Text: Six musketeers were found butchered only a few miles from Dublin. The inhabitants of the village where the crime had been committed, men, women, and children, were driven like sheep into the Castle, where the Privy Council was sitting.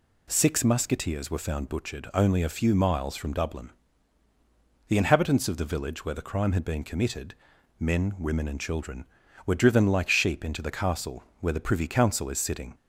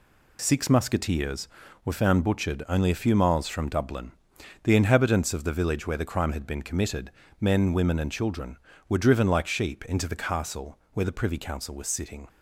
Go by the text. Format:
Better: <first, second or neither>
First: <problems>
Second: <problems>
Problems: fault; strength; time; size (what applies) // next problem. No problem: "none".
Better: second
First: says "is" for "was"; at 12.2 s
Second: none